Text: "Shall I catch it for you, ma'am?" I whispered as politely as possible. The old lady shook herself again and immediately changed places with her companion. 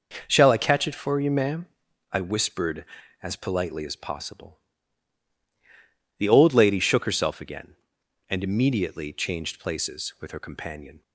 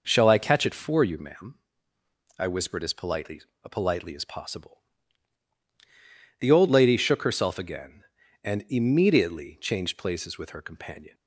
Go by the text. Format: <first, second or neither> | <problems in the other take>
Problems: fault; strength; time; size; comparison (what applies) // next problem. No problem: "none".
first | says "politely" twice; at 3.7 s